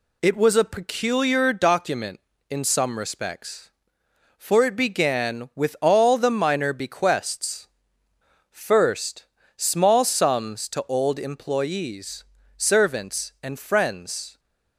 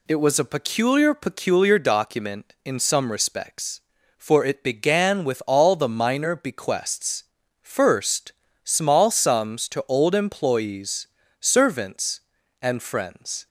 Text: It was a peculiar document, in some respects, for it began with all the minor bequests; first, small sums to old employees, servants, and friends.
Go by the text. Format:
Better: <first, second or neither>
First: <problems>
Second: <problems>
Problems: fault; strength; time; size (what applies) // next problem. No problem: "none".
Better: first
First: none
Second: says "peculiar" twice; at 1.1 s